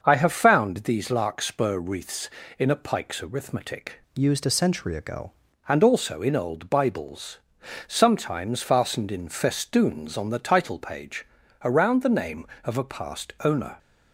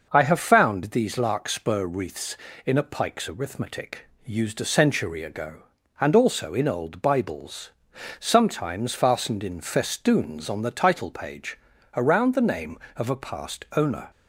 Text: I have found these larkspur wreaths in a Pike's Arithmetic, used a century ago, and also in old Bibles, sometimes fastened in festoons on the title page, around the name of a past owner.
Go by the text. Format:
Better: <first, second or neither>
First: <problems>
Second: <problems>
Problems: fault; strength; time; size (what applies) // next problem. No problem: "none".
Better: second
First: starts louder than the rest; until 1.0 s; 6.5 dB // changes voice from "used" to "ago"; from 4.1 to 5.3 s; 1.2 s long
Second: none